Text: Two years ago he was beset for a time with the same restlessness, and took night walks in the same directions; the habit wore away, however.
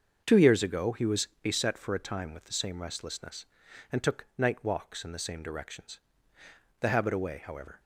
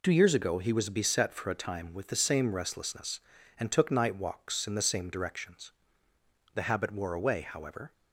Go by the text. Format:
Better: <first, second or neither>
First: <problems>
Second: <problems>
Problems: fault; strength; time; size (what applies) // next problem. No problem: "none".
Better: second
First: starts louder than the rest; until 1.2 s; 6.5 dB // skips "wore"; at 7.1 s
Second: none